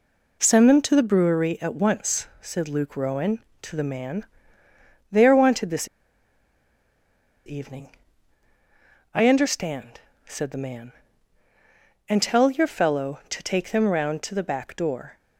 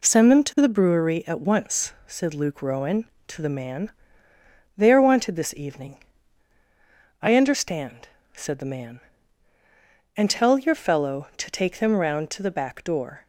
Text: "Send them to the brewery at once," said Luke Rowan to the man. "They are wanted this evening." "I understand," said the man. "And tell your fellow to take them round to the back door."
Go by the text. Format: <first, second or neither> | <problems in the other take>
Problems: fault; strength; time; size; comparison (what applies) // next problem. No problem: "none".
second | pauses between "this" and "evening"; strong; at 5.8 s; 1.6 s long